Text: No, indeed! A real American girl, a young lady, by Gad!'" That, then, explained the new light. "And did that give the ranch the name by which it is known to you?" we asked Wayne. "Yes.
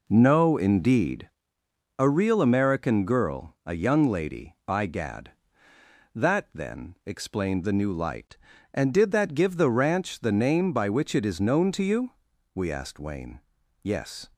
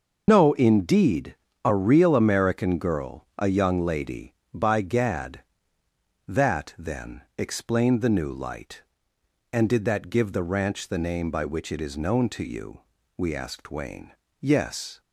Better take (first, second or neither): first